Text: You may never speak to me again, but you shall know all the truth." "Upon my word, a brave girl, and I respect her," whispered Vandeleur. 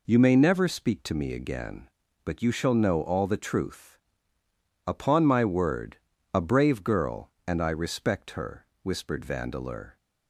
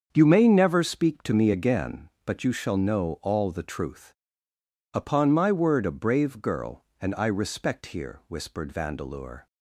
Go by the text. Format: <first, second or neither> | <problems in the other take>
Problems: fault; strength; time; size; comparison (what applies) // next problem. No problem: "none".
first | starts louder than the rest; until 1.1 s; 7 dB // says "here" for "her"; at 7.9 s